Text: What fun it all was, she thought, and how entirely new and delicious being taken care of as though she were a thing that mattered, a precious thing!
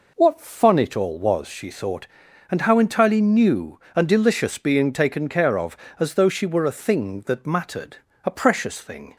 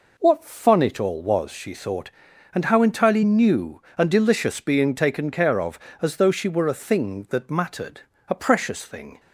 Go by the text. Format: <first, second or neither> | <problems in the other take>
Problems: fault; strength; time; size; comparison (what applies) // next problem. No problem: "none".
neither | none